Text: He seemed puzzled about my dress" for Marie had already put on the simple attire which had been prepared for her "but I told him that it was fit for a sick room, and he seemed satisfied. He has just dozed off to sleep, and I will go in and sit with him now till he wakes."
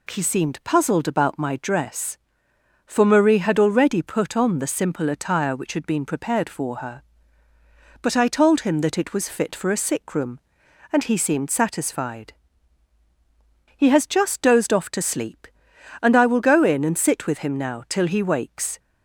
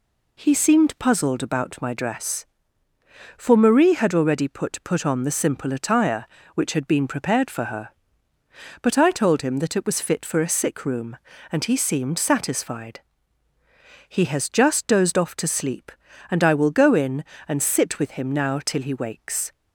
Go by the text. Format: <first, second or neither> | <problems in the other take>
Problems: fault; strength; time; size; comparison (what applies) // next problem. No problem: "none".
first | says "put" twice; at 4.8 s